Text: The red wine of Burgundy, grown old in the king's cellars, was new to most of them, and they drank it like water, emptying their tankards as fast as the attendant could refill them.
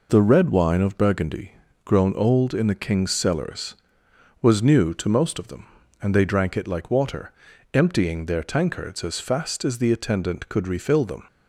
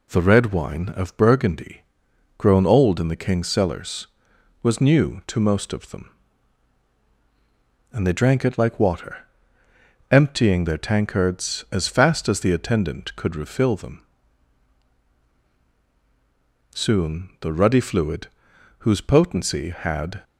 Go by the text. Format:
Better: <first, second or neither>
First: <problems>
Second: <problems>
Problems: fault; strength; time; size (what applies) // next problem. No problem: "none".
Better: first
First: none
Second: goes on to say "Soon the ruddy fluid whose potency had"; strong; from 16.7 s on; 3.5 s long